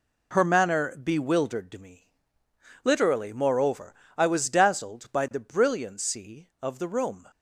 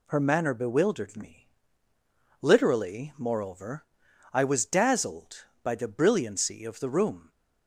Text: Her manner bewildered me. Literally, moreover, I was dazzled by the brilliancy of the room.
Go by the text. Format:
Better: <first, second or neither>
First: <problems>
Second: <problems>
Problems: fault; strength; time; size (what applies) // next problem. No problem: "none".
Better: neither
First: none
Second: none